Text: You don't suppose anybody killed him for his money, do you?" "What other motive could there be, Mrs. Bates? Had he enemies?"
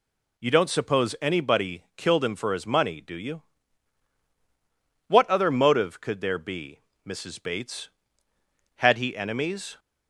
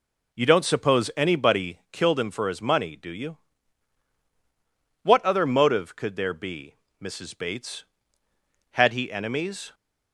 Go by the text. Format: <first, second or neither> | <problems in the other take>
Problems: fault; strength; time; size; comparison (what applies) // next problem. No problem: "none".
first | starts louder than the rest; noticeable; until 2.0 s; 4.5 dB